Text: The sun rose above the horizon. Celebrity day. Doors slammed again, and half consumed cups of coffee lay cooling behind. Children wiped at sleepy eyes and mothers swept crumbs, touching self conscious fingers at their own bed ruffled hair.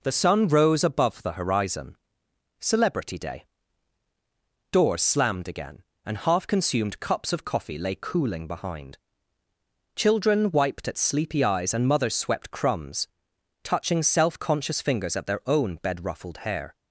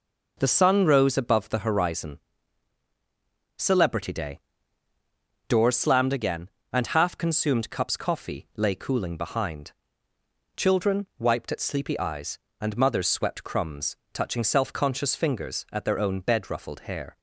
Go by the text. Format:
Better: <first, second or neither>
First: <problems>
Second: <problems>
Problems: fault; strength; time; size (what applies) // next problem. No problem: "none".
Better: first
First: none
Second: skips "of"; at 7.9 s